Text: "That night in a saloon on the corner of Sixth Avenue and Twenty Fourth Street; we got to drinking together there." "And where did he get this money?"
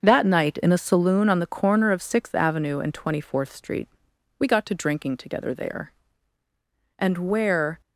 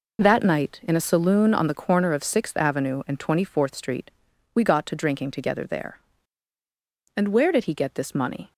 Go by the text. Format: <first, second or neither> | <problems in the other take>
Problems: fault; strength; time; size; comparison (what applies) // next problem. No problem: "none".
second | starts louder than the rest; until 1.0 s; 6.5 dB // stops before "did he get this money"; at 7.8 s